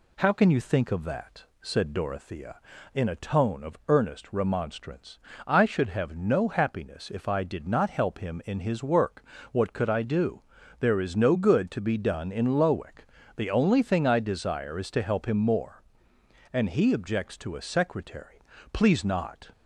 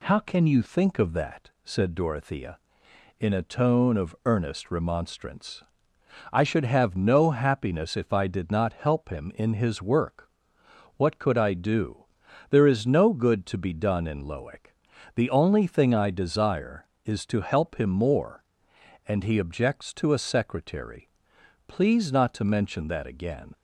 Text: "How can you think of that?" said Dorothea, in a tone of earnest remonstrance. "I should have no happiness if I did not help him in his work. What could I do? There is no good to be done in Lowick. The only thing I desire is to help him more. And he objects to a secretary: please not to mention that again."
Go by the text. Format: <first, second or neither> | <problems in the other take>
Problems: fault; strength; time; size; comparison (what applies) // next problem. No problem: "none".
second | stops before "to mention that again"; at 19.5 s